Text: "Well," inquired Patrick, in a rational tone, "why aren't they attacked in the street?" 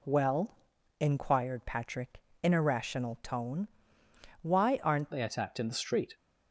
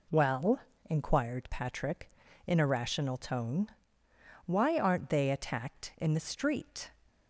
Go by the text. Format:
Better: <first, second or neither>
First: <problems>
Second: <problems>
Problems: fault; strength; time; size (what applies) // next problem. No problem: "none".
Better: second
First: changes voice at "they"; from 5.1 s on; 1.0 s long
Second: none